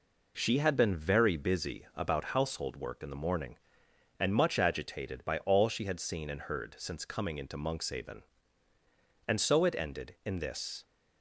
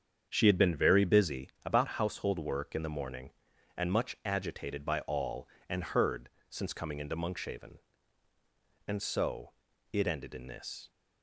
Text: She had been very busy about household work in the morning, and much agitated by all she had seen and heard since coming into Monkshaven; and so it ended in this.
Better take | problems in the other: first | starts louder than the rest; strong; until 1.3 s; 7.5 dB // pauses between "busy" and "about"; slight; at 1.4 s; 0.16 s long // skips "she had seen"; at 5.5 s // pauses between "heard" and "since"; slight; at 6.2 s; 0.20 s long // pauses between "so" and "it"; at 9.5 s; 0.38 s long

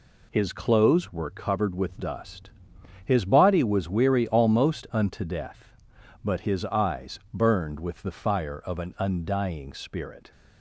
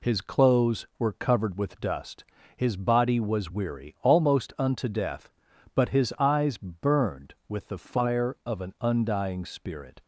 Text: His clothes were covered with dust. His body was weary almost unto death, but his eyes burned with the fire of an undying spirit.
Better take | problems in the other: neither | none

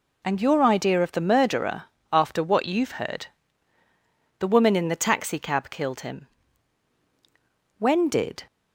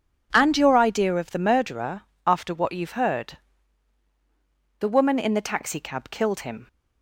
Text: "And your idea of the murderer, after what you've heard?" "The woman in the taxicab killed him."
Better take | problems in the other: second | goes on to say "When did"; noticeable; from 7.7 s on; 0.66 s long

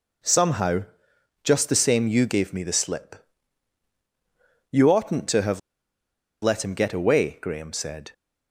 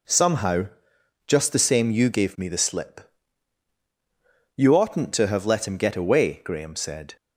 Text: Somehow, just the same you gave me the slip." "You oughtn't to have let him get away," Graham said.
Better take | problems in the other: second | pauses between "have" and "let"; noticeable; at 5.5 s; 0.83 s long

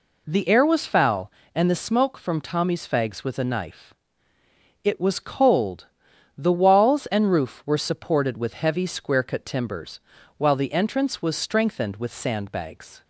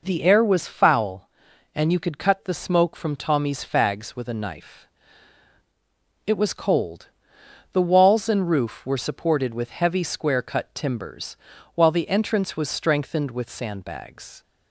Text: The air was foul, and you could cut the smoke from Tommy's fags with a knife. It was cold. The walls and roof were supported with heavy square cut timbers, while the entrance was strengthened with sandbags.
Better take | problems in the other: second | skips "you could cut"; at 1.6 s

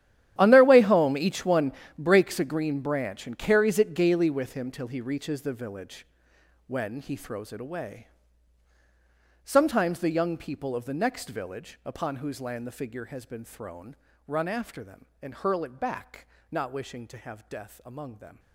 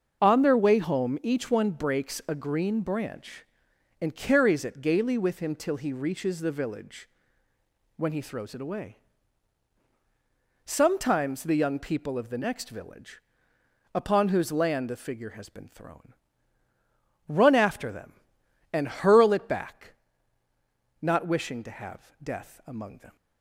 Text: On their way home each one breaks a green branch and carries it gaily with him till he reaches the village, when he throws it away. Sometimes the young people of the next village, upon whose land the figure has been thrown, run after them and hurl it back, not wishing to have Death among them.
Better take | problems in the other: second | gets quieter; strong; throughout; 16 dB // starts louder than the rest; strong; until 1.3 s; 11.5 dB; also in the second // pauses between "one" and "breaks"; slight; at 1.7 s; 0.24 s long

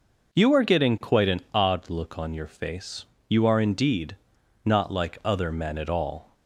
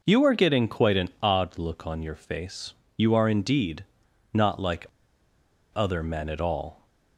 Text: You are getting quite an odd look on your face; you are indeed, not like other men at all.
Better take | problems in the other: first | pauses between "like" and "other"; noticeable; at 4.8 s; 0.87 s long

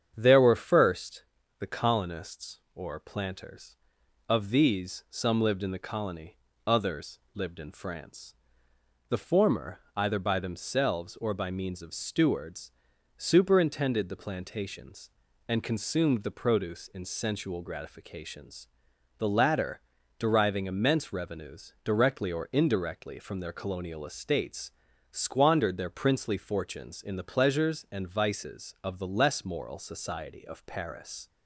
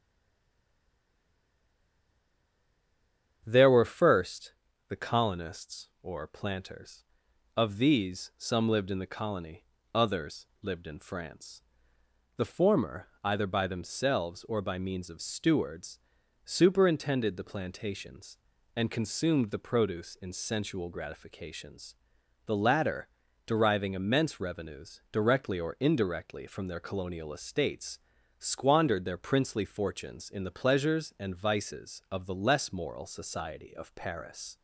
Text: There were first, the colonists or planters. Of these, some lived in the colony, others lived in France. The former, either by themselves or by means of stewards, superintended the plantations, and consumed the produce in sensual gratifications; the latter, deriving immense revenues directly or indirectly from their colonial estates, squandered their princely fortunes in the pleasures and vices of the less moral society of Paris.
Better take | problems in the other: first | stays silent before the first word; strong; until 3.4 s; 3.4 s long // starts louder than the rest; strong; until 4.4 s; 8.5 dB; strong in the first // pauses between "others" and "lived"; slight; at 10.4 s; 0.16 s long; slight in the first

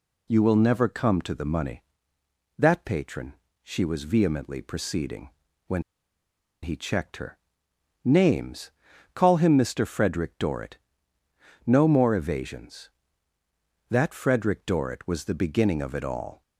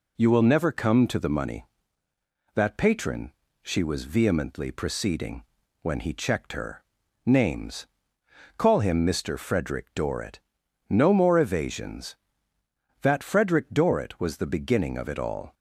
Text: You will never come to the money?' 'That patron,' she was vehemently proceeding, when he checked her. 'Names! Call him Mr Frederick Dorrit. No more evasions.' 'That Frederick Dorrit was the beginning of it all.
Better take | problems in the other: second | pauses between "when" and "he"; noticeable; at 5.8 s; 0.81 s long

